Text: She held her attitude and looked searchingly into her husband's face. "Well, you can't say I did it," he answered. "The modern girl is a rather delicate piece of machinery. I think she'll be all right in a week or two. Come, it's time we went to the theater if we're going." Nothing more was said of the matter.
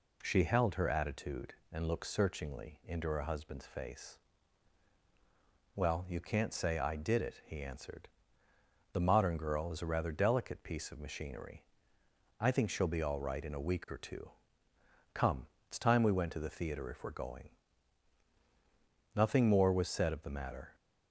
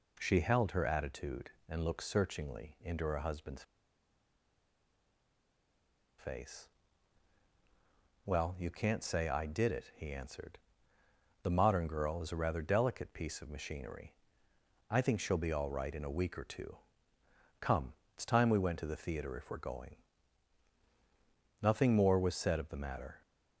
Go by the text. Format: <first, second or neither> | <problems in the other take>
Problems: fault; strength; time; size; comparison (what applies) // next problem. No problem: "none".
first | pauses between "husband's" and "face"; strong; at 3.6 s; 2.5 s long